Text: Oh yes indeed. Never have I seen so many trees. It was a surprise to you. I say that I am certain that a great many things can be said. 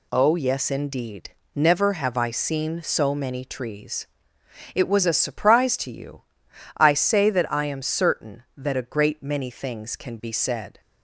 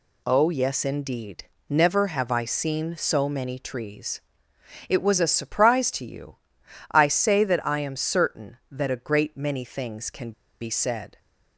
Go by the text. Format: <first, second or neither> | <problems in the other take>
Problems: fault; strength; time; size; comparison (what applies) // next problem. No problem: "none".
first | pauses between "can" and "be"; slight; at 10.3 s; 0.29 s long